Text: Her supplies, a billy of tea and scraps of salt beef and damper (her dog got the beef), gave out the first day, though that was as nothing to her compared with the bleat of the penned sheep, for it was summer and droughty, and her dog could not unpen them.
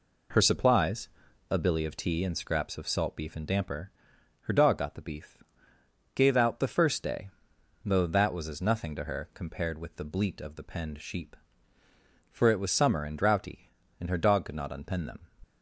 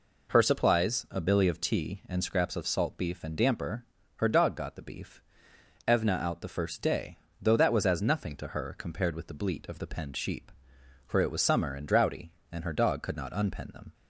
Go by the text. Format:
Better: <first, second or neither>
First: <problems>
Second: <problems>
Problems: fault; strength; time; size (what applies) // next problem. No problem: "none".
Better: first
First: none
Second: says "evna" for "gave"; at 5.8 s